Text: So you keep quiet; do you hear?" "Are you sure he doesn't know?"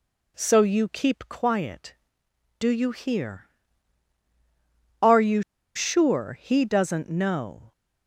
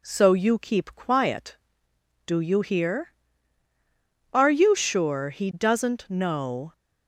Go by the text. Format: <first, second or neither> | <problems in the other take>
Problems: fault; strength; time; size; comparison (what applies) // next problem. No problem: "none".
second | pauses between "you" and "sure"; slight; at 5.4 s; 0.34 s long